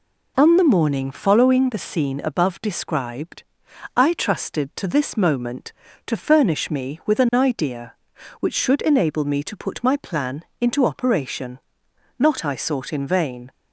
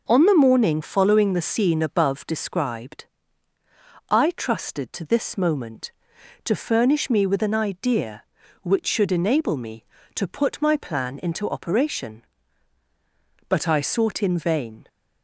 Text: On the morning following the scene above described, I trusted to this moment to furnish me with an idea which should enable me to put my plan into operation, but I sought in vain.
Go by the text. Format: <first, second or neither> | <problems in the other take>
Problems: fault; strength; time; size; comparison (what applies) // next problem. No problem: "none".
second | pauses between "plan" and "into"; slight; at 10.4 s; 0.16 s long // says "not" for "but"; at 12.1 s